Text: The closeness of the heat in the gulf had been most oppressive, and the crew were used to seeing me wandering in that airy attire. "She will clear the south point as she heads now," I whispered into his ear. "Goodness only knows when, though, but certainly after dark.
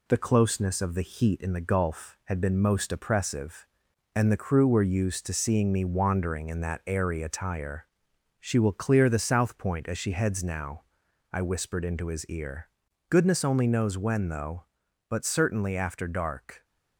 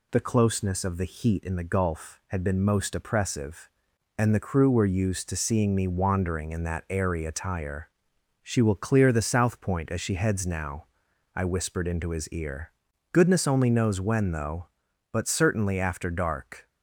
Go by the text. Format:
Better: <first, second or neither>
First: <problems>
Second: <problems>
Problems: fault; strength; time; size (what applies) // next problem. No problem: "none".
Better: second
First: gets quieter; slight; throughout; 2.5 dB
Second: none